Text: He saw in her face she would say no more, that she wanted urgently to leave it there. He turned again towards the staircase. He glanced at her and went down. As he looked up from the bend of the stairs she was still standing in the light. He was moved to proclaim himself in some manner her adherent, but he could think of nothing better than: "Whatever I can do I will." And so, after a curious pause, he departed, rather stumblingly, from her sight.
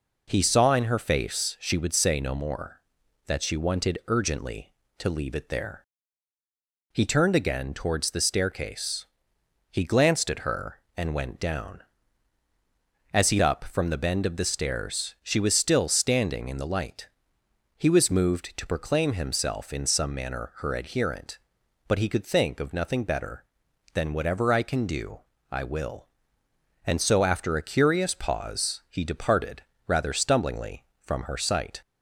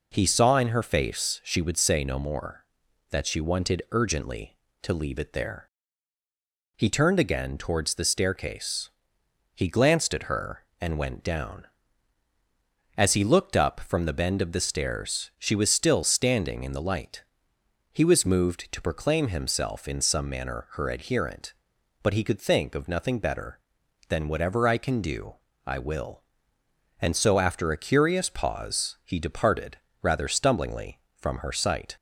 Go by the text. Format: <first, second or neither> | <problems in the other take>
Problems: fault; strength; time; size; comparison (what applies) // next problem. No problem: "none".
second | skips "looked"; at 13.4 s // pauses between "do" and "I"; slight; at 25.2 s; 0.30 s long; slight in the second